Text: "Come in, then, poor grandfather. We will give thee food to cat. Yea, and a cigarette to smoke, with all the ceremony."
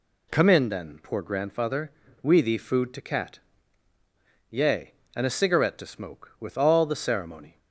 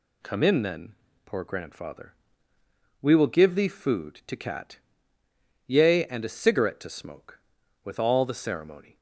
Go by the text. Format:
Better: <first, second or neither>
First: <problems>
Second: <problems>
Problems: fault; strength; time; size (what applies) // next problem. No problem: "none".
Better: second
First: skips "will give"; at 2.4 s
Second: none